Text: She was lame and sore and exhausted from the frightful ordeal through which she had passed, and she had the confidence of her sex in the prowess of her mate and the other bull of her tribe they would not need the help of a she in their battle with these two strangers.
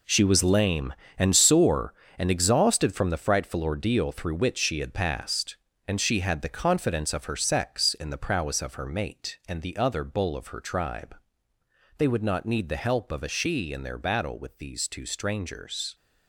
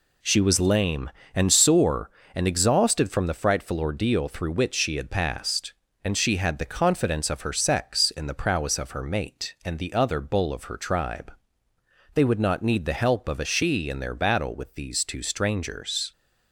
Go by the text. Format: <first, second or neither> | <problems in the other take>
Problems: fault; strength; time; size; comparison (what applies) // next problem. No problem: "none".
second | gets quieter; strong; throughout; 10.5 dB // pauses between "tribe" and "they"; noticeable; at 11.1 s; 0.82 s long; noticeable in the second